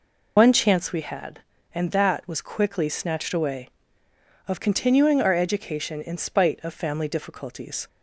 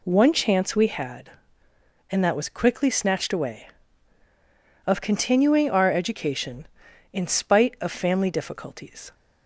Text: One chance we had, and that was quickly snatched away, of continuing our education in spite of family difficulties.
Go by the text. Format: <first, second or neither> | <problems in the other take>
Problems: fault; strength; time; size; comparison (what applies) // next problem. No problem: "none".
second | loses the start of "One"; at 0.3 s; 125 ms